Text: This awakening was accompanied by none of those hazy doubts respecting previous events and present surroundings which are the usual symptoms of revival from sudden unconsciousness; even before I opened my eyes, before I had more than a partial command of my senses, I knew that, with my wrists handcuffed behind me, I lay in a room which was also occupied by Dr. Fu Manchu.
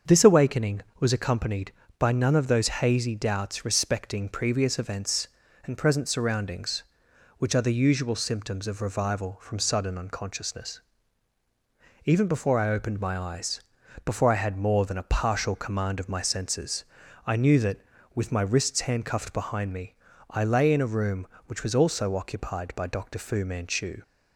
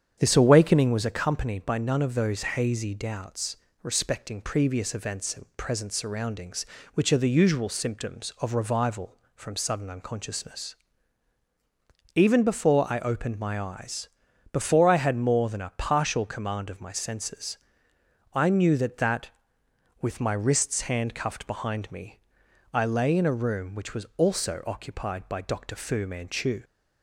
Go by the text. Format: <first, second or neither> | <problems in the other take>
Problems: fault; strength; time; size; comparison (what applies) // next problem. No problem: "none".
first | starts louder than the rest; strong; until 1.2 s; 8 dB; also in the first // pauses between "doubts" and "respecting"; slight; at 3.5 s; 0.28 s long // says "that" twice; at 18.9 s